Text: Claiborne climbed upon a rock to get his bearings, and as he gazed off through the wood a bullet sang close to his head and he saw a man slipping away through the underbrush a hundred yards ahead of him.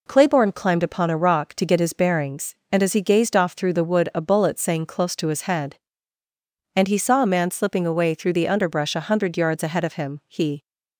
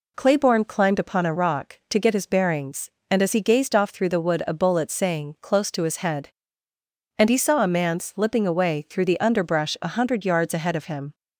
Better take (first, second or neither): second